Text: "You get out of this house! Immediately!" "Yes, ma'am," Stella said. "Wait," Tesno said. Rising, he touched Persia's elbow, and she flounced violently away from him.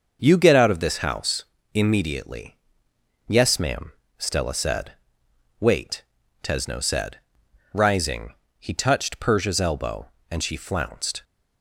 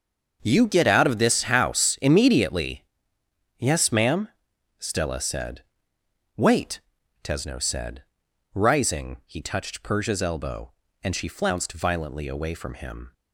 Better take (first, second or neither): second